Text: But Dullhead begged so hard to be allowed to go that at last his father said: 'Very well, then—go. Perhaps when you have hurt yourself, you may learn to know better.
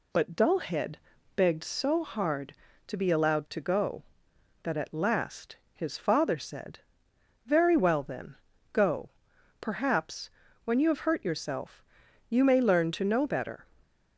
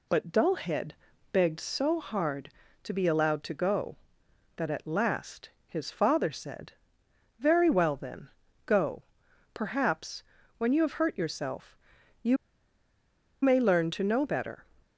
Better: first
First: pauses between "Dullhead" and "begged"; at 0.9 s; 0.38 s long // pauses between "last" and "his"; slight; at 5.5 s; 0.16 s long // pauses between "Perhaps" and "when"; slight; at 10.3 s; 0.32 s long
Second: pauses between "Dullhead" and "begged"; at 0.9 s; 0.38 s long // pauses between "last" and "his"; slight; at 5.4 s; 0.16 s long // pauses between "Perhaps" and "when"; slight; at 10.2 s; 0.32 s long // pauses between "you" and "may"; at 12.3 s; 1.0 s long

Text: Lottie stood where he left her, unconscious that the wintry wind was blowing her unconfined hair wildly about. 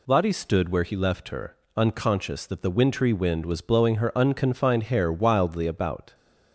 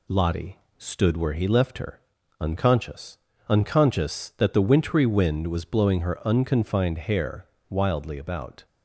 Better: first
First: none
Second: pauses between "Lottie" and "stood"; slight; at 0.5 s; 0.20 s long // says "unconscious" twice; at 3.4 s // pauses between "hair" and "wildly"; slight; at 7.4 s; 0.24 s long

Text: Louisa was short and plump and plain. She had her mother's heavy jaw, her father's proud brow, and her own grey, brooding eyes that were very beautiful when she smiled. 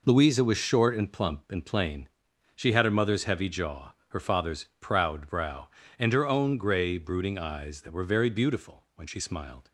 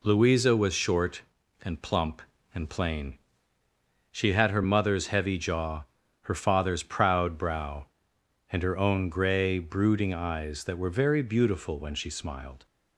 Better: neither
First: none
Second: none

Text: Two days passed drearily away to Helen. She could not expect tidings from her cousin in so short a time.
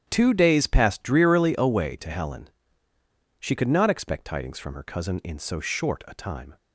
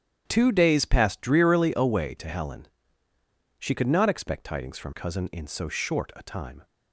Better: first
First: starts louder than the rest; strong; until 1.0 s; 10 dB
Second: starts louder than the rest; strong; until 1.2 s; 10 dB // skips "her"; at 4.9 s

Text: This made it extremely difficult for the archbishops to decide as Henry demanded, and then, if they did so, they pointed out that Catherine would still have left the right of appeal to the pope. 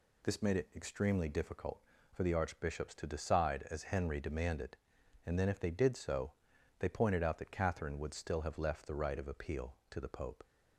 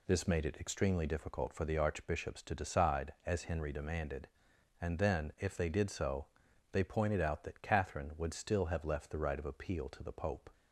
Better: neither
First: none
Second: none

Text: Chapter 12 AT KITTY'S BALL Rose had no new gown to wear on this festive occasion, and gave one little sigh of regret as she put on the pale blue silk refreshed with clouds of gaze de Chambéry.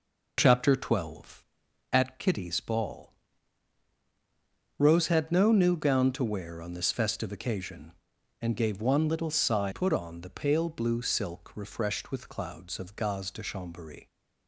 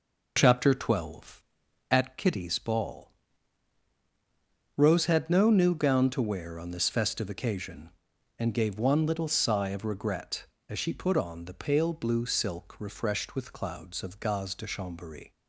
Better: second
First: pauses between "BALL" and "Rose"; strong; at 3.1 s; 1.6 s long // skips "of regret as she"; at 9.7 s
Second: pauses between "BALL" and "Rose"; strong; at 3.1 s; 1.6 s long

